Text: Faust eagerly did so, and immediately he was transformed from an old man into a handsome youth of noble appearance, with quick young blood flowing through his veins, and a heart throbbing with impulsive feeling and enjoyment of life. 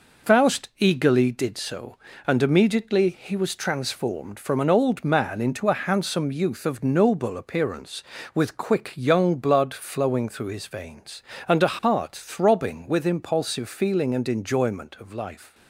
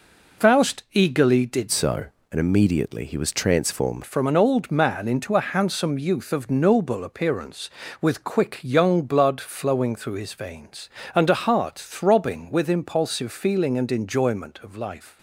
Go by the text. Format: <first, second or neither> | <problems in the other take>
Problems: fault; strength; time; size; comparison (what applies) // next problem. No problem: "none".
first | changes voice from "so" to "transformed"; from 1.7 to 4.0 s; 2.3 s long